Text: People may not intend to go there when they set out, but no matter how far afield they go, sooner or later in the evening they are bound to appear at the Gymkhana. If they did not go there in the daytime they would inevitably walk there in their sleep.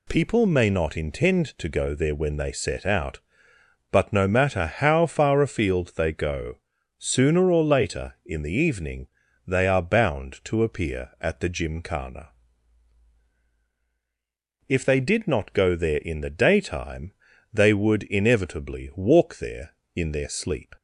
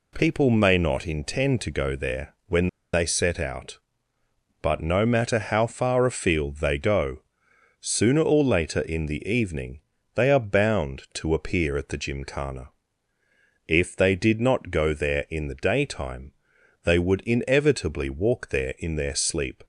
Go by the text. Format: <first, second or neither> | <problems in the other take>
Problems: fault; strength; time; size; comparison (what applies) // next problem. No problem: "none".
first | pauses between "when" and "they"; slight; at 2.6 s; 0.25 s long // pauses between "evening" and "they"; slight; at 9.7 s; 0.34 s long; also in the first // pauses between "daytime" and "they"; noticeable; at 16.3 s; 0.52 s long; also in the first